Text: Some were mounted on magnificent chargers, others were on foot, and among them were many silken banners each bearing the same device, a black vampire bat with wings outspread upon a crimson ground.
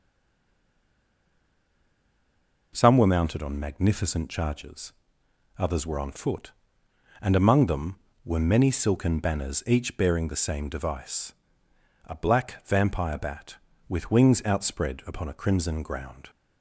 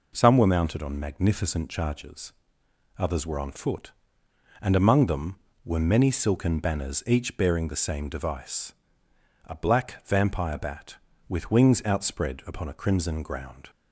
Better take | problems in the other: second | stays silent before the first word; strong; until 2.7 s; 2.7 s long

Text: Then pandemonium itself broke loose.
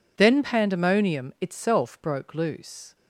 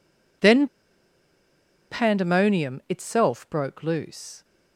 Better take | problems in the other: first | pauses between "Then" and "pandemonium"; at 0.6 s; 1.2 s long

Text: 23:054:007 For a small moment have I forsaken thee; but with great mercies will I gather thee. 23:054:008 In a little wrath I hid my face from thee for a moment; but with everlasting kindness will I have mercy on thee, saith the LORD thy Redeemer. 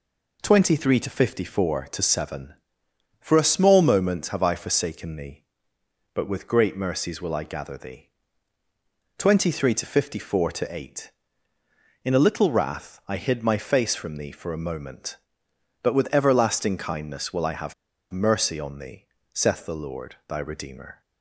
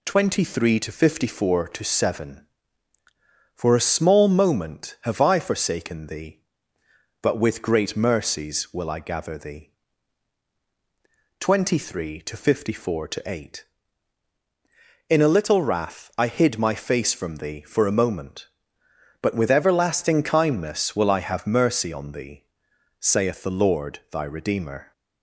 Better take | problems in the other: second | pauses between "have" and "mercy"; at 17.7 s; 0.38 s long

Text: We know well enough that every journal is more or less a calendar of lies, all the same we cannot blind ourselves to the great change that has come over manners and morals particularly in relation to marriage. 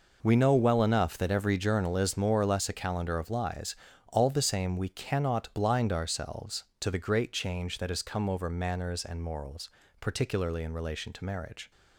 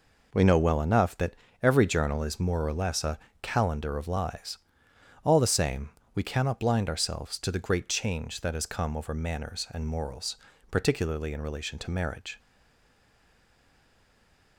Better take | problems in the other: first | pauses between "that" and "every"; slight; at 1.3 s; 0.28 s long // pauses between "a" and "calendar"; slight; at 3.1 s; 0.22 s long // pauses between "same" and "we"; slight; at 5.8 s; 0.26 s long // pauses between "morals" and "particularly"; slight; at 10.3 s; 0.34 s long; slight in the first // stays silent after the last word; from 12.3 s on; 2.2 s long

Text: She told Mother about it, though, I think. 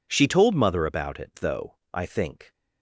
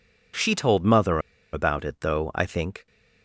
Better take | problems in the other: first | pauses between "Mother" and "about"; slight; at 1.2 s; 0.32 s long

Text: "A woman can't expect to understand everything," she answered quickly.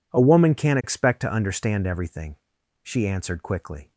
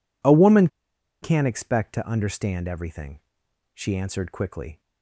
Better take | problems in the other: first | pauses between "woman" and "can't"; noticeable; at 0.6 s; 0.54 s long

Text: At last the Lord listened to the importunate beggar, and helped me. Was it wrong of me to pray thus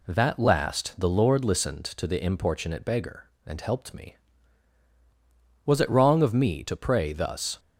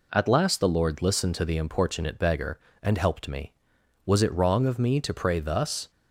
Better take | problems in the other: second | says "That" for "At"; at 0.0 s

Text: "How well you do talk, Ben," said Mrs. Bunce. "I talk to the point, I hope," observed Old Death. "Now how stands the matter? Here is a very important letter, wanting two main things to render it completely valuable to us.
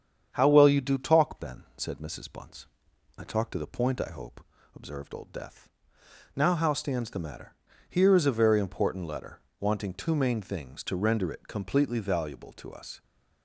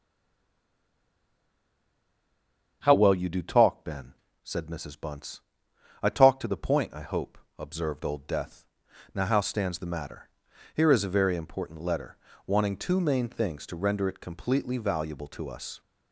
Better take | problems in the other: first | stays silent before the first word; strong; until 2.8 s; 2.8 s long // starts louder than the rest; strong; until 3.8 s; 7.5 dB; strong in the first

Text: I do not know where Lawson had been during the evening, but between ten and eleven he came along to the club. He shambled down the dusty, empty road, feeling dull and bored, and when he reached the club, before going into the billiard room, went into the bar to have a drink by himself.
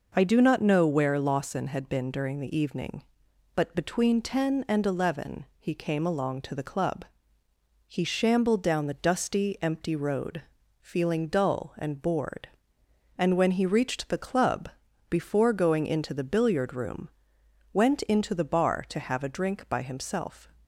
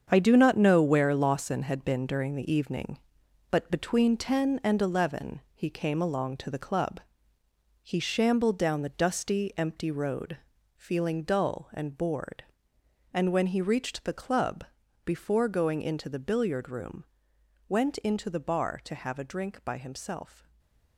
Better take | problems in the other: first | gets quieter; strong; throughout; 9 dB // stays silent after the last word; slight; from 20.3 s on; 0.6 s long

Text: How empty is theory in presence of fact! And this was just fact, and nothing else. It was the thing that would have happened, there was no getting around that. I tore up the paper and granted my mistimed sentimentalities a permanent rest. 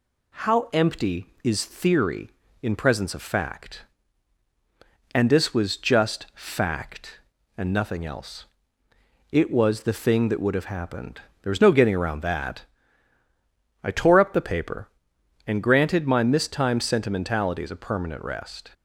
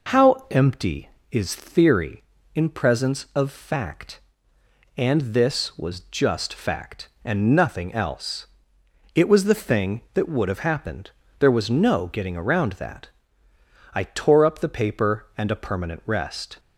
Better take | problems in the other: first | skips "granted my mistimed sentimentalities"; at 15.5 s

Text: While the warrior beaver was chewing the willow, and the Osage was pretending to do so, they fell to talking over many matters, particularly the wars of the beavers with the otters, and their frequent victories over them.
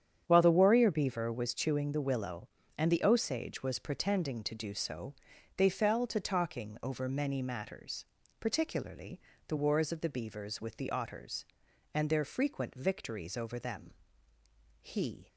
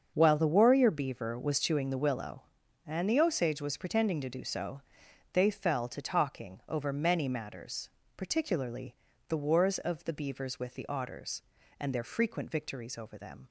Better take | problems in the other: second | starts louder than the rest; strong; until 1.2 s; 8.5 dB; also in the second // pauses between "particularly" and "the"; slight; at 9.1 s; 0.28 s long; slight in the second // goes on to say "He"; slight; from 14.7 s on; 0.48 s long

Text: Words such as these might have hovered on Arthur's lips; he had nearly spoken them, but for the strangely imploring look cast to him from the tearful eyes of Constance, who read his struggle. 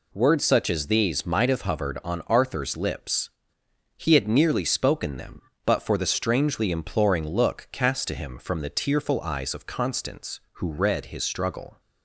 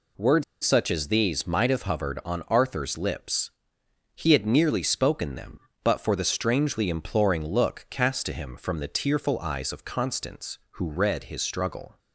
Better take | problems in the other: first | pauses between "Words" and "such"; slight; at 0.4 s; 0.20 s long

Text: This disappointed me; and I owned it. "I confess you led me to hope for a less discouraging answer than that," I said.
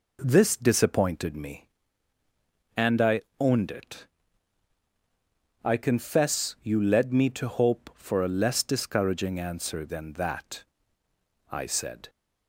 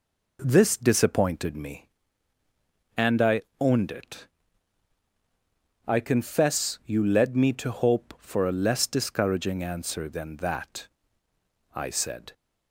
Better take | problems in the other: neither | pauses between "I" and "owned"; slight; the same in both

